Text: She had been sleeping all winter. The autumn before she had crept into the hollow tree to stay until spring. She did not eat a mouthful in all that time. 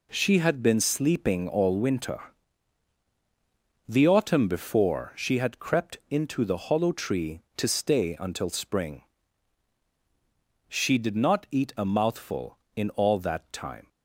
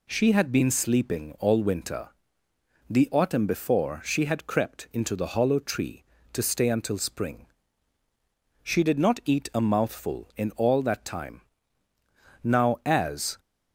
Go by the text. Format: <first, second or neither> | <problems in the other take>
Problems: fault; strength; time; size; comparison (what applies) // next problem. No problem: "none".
first | goes on to say "Now as"; noticeable; from 12.4 s on; 0.96 s long